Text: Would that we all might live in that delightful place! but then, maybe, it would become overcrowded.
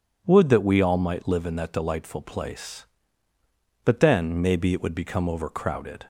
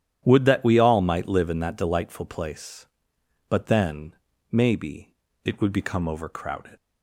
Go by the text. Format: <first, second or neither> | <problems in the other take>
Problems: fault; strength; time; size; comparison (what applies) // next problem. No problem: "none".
first | starts louder than the rest; strong; until 1.2 s; 10.5 dB // leaves "overcrowded" unfinished; at 6.7 s; 110 ms